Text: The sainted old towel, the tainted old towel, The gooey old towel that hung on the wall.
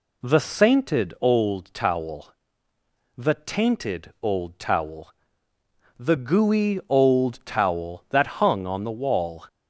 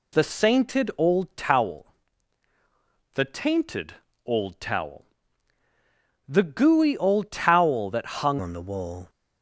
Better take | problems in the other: first | pauses between "tainted" and "old"; slight; at 3.9 s; 0.30 s long // changes voice at "on"; from 8.3 s on; 0.7 s long

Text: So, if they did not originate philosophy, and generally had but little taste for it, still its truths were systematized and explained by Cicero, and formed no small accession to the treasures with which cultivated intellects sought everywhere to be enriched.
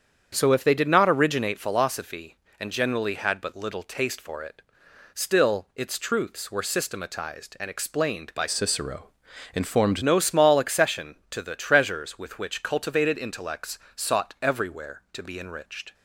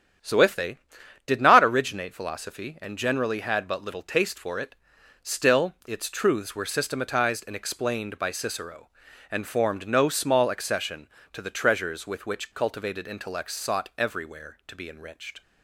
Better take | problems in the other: second | starts louder than the rest; strong; until 1.3 s; 8 dB; strong in the second // changes voice from "Cicero" to "formed"; from 8.4 to 10.0 s; 1.6 s long // pauses between "intellects" and "sought"; slight; at 13.7 s; 0.18 s long

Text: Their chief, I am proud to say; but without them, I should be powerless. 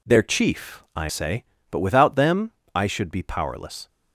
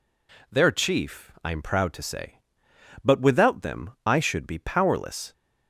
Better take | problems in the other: second | skips "am proud to"; at 1.0 s

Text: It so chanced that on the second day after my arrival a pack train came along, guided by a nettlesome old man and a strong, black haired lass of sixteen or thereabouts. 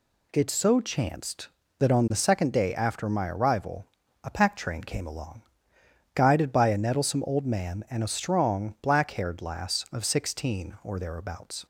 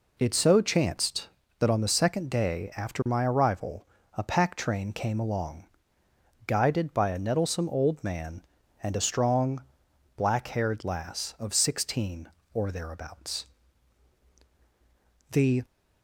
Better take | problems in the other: first | pauses between "arrival" and "a"; slight; at 3.8 s; 0.32 s long; also in the first // goes on to say "The"; slight; from 15.3 s on; 0.34 s long

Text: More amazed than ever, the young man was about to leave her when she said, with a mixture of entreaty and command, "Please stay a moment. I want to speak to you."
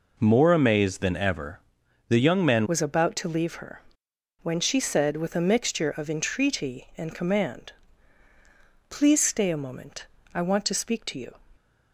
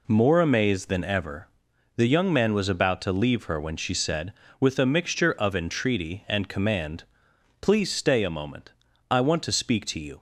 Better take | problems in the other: second | changes voice at "was"; from 2.6 s on; 8.7 s long // pauses between "her" and "when"; noticeable; at 3.8 s; 0.60 s long

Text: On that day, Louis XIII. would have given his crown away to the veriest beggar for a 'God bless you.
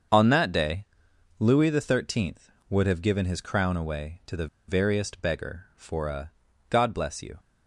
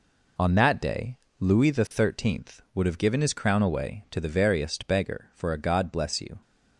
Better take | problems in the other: second | starts louder than the rest; until 1.6 s; 7 dB // pauses between "the" and "veriest"; slight; at 4.4 s; 0.21 s long // pauses between "a" and "God"; at 6.2 s; 0.40 s long

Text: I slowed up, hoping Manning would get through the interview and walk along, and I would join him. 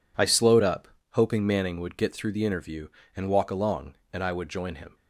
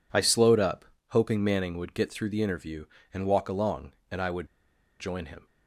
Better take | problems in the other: first | pauses between "would" and "join"; noticeable; at 4.4 s; 0.54 s long

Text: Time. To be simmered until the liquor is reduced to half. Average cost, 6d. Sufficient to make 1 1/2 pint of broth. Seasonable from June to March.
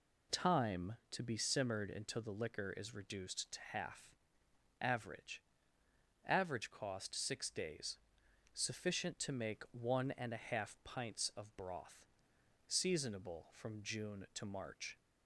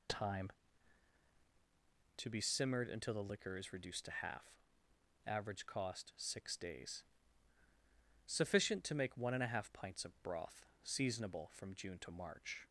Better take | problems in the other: second | says "Average" twice; at 6.2 s

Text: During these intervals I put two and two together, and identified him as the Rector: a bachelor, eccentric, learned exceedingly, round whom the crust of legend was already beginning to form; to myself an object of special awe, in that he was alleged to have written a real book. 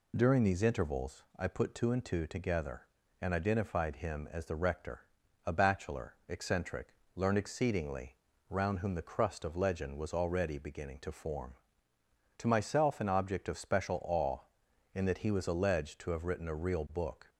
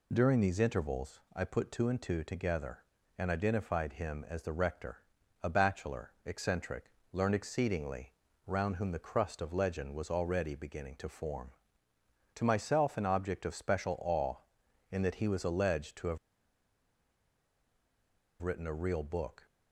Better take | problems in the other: first | pauses between "have" and "written"; strong; at 16.1 s; 2.2 s long

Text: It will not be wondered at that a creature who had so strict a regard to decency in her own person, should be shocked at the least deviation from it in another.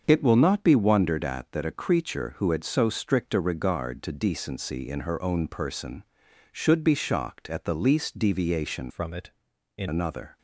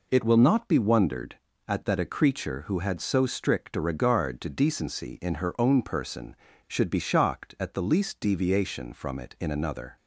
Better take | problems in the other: second | starts louder than the rest; until 1.0 s; 6.5 dB // changes voice from "from" to "in"; from 8.8 to 9.8 s; 1.0 s long

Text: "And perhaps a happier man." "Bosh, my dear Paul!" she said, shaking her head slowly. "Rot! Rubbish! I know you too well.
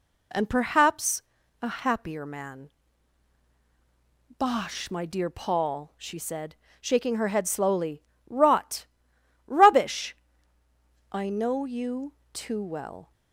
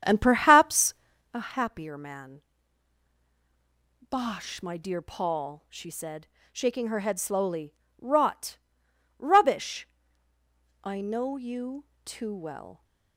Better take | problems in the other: first | starts louder than the rest; strong; until 1.3 s; 8.5 dB // pauses between "perhaps" and "a"; at 0.9 s; 0.40 s long; also in the first // pauses between "you" and "too"; slight; at 11.8 s; 0.18 s long; slight in the first

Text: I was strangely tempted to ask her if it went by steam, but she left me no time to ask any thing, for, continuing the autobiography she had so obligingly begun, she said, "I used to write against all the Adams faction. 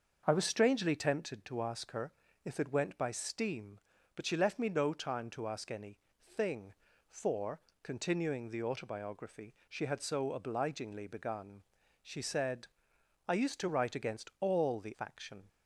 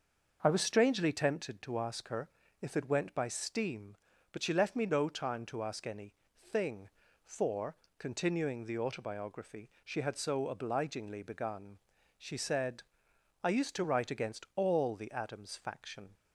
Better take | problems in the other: second | starts louder than the rest; until 1.2 s; 6.5 dB; also in the second // pauses between "her" and "if"; slight; at 2.1 s; 0.36 s long; slight in the second // pauses between "any" and "thing"; slight; at 5.9 s; 0.28 s long; slight in the second // skips "Adams"; at 14.9 s

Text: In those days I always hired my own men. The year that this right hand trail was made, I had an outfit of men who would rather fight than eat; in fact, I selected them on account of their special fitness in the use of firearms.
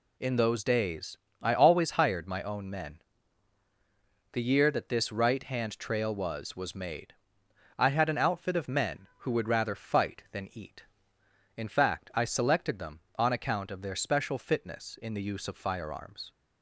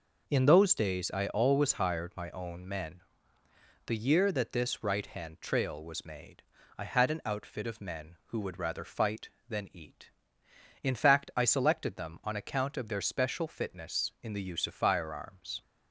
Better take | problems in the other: second | pauses between "days" and "I"; slight; at 1.1 s; 0.24 s long // says "was" twice; at 6.5 s

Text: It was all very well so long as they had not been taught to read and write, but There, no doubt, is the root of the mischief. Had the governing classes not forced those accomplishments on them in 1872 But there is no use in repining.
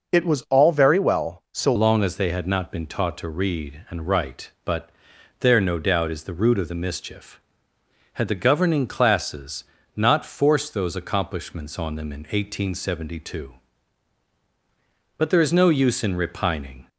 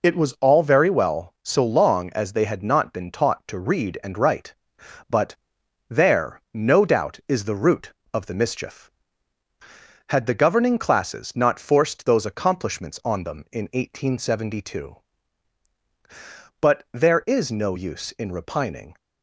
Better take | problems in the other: second | changes voice at "long"; from 1.7 s on; 15.1 s long // pauses between "but" and "There"; noticeable; at 4.9 s; 0.50 s long; noticeable in the second // pauses between "classes" and "not"; slight; at 9.6 s; 0.32 s long

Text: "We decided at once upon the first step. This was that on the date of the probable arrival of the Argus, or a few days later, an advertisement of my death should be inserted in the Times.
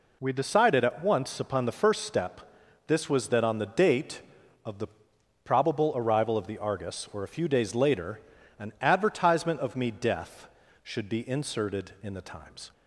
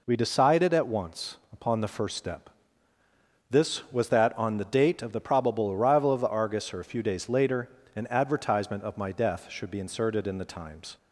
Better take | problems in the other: second | pauses between "the" and "probable"; noticeable; at 4.8 s; 0.56 s long // says "me" for "my"; at 9.7 s

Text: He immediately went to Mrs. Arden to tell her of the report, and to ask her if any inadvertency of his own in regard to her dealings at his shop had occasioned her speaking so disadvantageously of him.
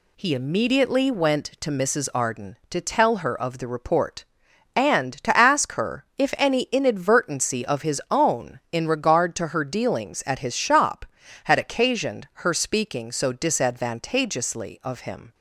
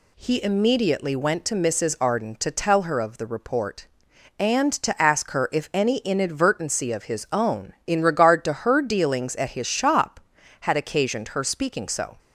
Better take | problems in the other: first | stops before "disadvantageously of him"; at 12.1 s

